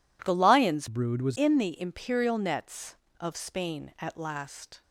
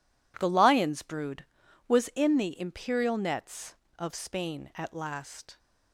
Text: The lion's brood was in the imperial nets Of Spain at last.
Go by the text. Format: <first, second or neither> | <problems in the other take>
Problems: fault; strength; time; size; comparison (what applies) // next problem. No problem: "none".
second | changes voice from "brood" to "was"; from 0.8 to 1.3 s; 0.5 s long